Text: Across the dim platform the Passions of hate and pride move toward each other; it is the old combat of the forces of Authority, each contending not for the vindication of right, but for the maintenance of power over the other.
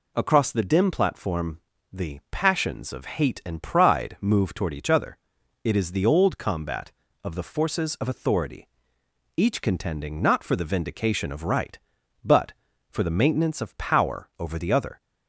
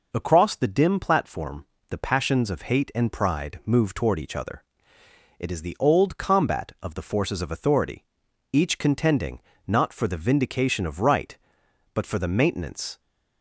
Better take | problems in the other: first | pauses between "platform" and "the"; slight; at 1.6 s; 0.24 s long; slight in the first // pauses between "contending" and "not"; slight; at 9.4 s; 0.26 s long // stops before "of power over the other"; at 12.9 s

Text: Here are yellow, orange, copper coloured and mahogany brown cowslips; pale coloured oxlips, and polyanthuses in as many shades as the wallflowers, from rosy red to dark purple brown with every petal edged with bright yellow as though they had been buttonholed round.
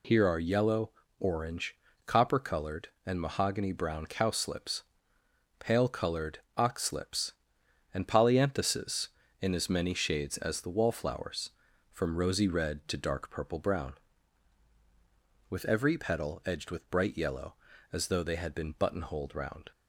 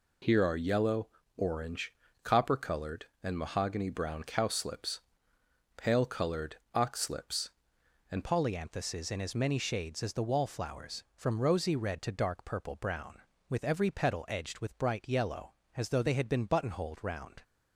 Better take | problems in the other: first | pauses between "coloured" and "oxlips"; slight; at 6.5 s; 0.18 s long; slight in the first // changes voice at "polyanthuses"; from 8.2 s on; 9.2 s long

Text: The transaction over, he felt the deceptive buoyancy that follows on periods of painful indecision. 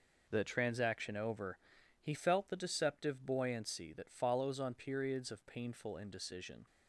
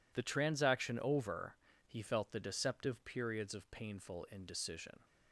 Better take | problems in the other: first | skips "buoyancy that follows on"; at 3.0 s

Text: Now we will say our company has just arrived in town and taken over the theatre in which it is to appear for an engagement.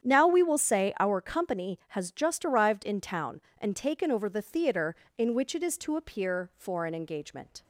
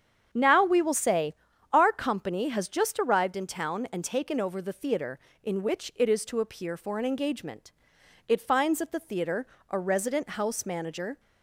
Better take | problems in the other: first | starts louder than the rest; strong; until 1.3 s; 8 dB; strong in the first // pauses between "say" and "our"; at 1.3 s; 0.38 s long // goes on to say "It finds at the theatre a resident house manager"; strong; from 8.2 s on; 2.9 s long

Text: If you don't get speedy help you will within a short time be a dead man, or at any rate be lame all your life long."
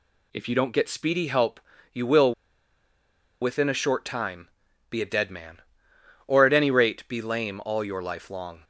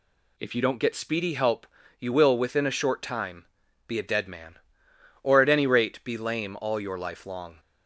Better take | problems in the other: second | pauses between "help" and "you"; slight; at 1.5 s; 0.32 s long; slight in the second // pauses between "will" and "within"; at 2.3 s; 1.0 s long // pauses between "time" and "be"; at 4.4 s; 0.42 s long; also in the second

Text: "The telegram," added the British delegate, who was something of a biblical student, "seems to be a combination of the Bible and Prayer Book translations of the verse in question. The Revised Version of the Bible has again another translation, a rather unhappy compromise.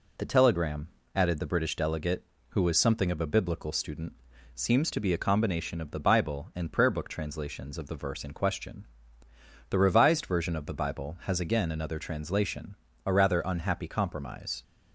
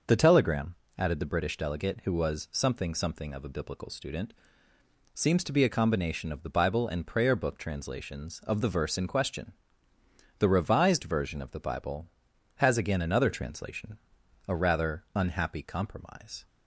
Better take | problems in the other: first | says "something" twice; at 2.9 s

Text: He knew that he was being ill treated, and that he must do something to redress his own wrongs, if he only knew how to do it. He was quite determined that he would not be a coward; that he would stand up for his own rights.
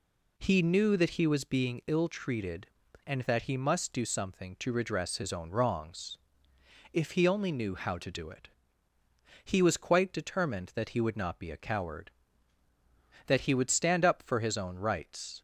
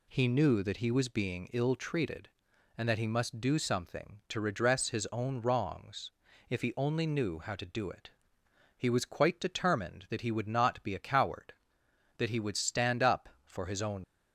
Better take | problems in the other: first | stops before "rights"; at 14.0 s

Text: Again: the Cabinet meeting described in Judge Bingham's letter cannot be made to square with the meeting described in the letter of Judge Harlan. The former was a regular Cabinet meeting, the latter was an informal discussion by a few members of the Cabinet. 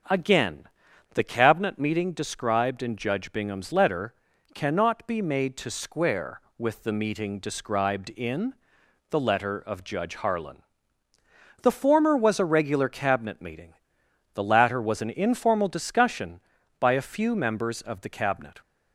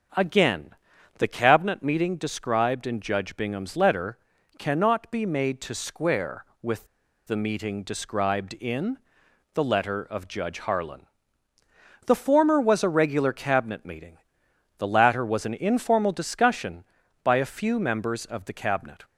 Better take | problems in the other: first | starts louder than the rest; until 1.6 s; 7 dB; also in the first // pauses between "letter" and "cannot"; at 4.1 s; 0.40 s long; also in the first // pauses between "with" and "the"; at 6.8 s; 0.40 s long // pauses between "in" and "the"; noticeable; at 8.9 s; 0.56 s long; noticeable in the first

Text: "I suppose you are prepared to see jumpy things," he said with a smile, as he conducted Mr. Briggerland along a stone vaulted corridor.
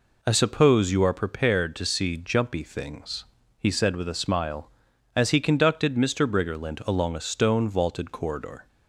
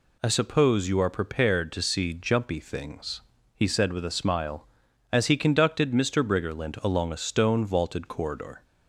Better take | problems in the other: second | starts louder than the rest; until 1.2 s; 4 dB

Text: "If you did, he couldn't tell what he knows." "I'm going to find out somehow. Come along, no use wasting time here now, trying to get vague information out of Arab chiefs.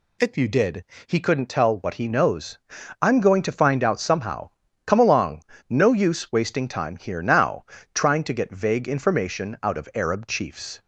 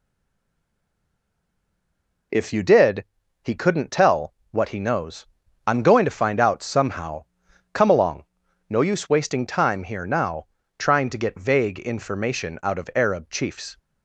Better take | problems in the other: first | stays silent before the first word; until 2.3 s; 2.3 s long // pauses between "tell" and "what"; slight; at 4.3 s; 0.18 s long

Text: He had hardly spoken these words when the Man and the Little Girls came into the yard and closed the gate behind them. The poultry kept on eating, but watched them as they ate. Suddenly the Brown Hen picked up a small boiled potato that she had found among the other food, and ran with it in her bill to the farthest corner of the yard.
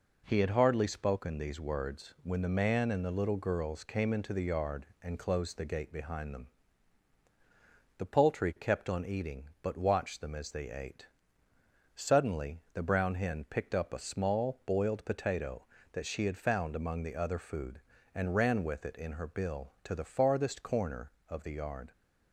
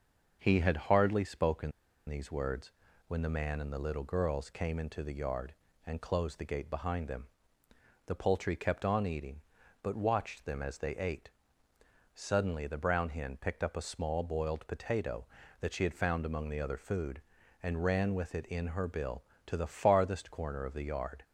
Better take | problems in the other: first | pauses between "spoken" and "these"; at 1.7 s; 0.37 s long // pauses between "words" and "when"; slight; at 2.7 s; 0.36 s long

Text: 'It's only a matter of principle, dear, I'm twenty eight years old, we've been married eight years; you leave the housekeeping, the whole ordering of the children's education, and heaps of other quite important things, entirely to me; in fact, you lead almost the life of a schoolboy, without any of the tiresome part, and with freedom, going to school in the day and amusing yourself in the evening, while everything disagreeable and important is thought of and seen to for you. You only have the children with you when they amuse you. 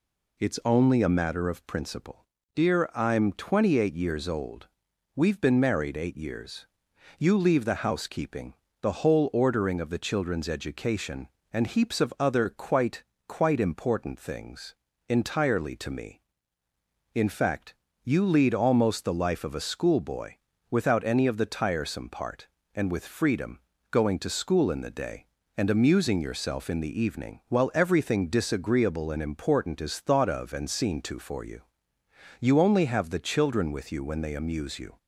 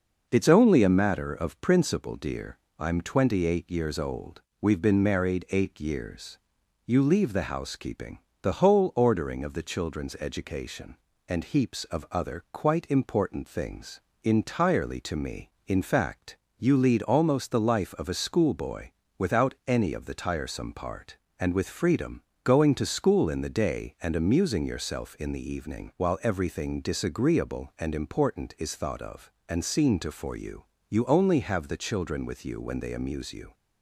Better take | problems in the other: second | says "quite" twice; at 13.2 s

